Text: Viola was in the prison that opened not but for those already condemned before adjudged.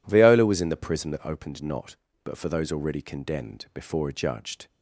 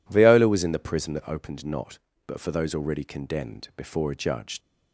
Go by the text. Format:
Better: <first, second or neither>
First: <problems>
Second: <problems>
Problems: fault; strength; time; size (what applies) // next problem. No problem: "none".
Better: first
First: none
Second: leaves "adjudged" unfinished; at 4.6 s; 90 ms